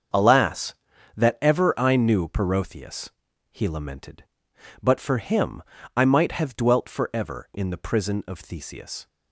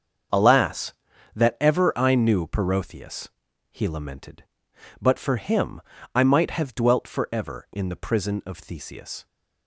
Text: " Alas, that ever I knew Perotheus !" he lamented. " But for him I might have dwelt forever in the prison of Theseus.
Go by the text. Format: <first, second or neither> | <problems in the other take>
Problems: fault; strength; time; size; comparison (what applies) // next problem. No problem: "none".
neither | starts louder than the rest; strong; the same in both // pauses between "him" and "I"; slight; the same in both